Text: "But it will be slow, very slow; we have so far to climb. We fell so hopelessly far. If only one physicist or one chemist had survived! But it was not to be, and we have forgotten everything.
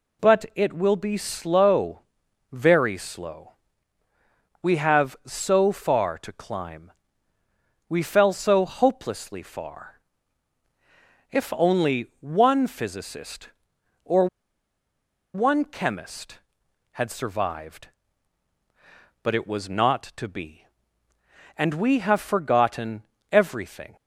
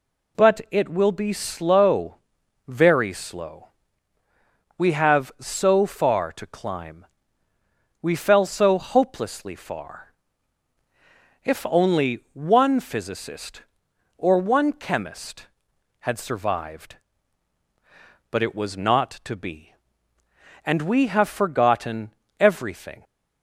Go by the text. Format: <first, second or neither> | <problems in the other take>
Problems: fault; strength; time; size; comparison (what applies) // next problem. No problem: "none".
second | pauses between "or" and "one"; at 14.2 s; 1.0 s long // pauses between "forgotten" and "everything"; slight; at 23.0 s; 0.28 s long; slight in the second